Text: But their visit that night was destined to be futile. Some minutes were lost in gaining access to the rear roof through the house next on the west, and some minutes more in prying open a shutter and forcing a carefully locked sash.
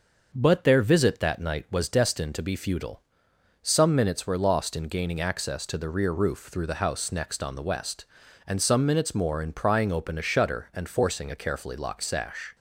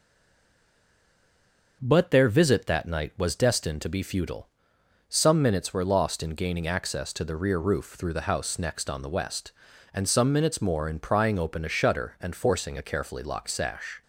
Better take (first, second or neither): first